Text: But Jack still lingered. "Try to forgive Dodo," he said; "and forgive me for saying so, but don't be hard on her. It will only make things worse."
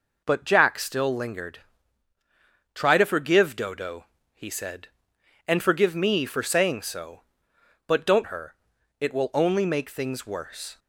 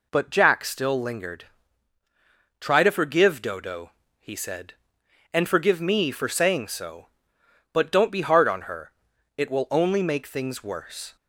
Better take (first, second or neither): second